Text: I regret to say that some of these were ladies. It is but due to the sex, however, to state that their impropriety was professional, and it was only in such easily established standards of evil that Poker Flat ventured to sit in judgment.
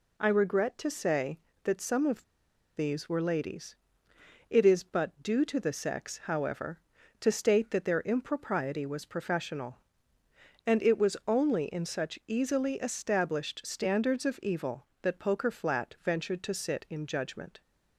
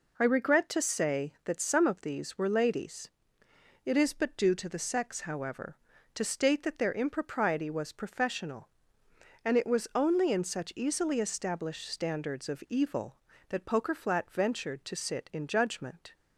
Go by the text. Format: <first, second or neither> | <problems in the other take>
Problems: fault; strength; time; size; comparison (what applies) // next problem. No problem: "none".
second | pauses between "of" and "these"; noticeable; at 2.2 s; 0.53 s long